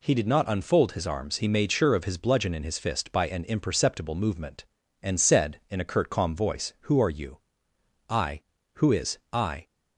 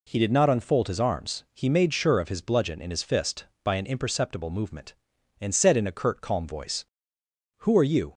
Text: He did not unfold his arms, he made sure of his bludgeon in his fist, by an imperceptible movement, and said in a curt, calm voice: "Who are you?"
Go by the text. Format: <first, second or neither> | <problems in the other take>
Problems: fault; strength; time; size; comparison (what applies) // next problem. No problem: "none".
second | goes on to say "I Who is I"; from 8.0 s on; 1.5 s long